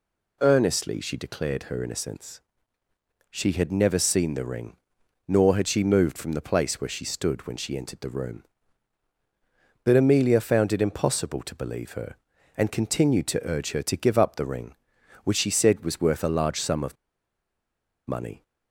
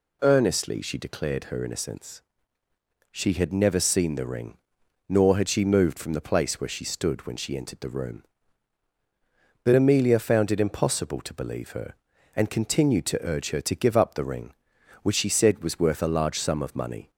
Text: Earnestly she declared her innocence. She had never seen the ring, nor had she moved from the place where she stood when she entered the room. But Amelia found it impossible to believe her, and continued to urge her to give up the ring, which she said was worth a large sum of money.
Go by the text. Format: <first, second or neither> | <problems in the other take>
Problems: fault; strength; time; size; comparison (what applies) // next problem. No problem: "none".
second | pauses between "of" and "money"; at 16.9 s; 1.1 s long